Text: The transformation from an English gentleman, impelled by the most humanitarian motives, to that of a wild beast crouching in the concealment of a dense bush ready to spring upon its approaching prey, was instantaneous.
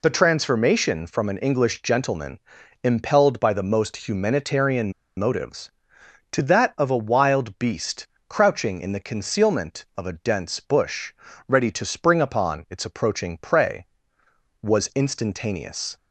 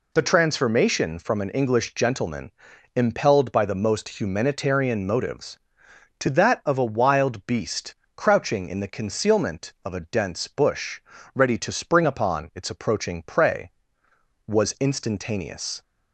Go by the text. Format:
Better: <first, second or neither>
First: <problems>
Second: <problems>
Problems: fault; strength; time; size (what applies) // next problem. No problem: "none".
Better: second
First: pauses between "humanitarian" and "motives"; slight; at 4.9 s; 0.24 s long // pauses between "beast" and "crouching"; slight; at 8.0 s; 0.22 s long // pauses between "bush" and "ready"; slight; at 11.1 s; 0.34 s long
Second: pauses between "beast" and "crouching"; slight; at 7.9 s; 0.22 s long // pauses between "bush" and "ready"; slight; at 11.0 s; 0.33 s long